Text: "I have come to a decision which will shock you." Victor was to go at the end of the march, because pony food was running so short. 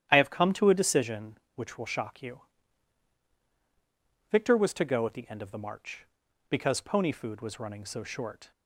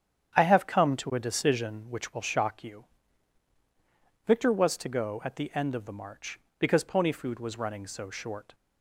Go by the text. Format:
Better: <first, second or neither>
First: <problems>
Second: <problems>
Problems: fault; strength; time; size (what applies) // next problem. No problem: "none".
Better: neither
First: starts louder than the rest; strong; until 1.1 s; 10.5 dB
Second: starts louder than the rest; strong; until 1.3 s; 9 dB